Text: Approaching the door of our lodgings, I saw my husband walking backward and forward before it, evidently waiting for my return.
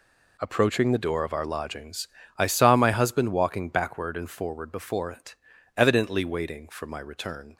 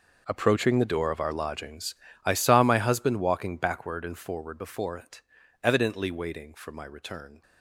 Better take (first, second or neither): first